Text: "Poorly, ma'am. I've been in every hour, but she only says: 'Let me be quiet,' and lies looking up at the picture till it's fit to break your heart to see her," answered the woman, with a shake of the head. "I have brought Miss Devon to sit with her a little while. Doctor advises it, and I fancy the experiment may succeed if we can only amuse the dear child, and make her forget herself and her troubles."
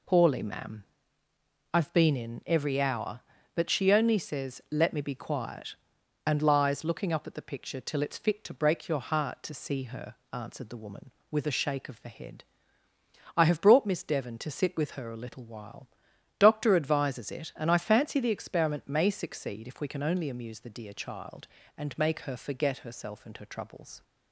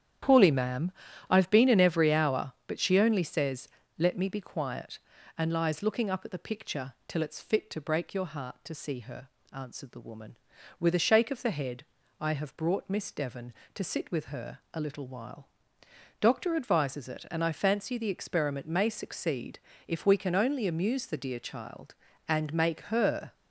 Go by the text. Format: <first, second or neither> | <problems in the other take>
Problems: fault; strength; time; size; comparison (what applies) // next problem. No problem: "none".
first | starts louder than the rest; strong; until 1.6 s; 10 dB // pauses between "succeed" and "if"; slight; at 19.5 s; 0.28 s long // stops before "forget herself and her troubles"; at 23.3 s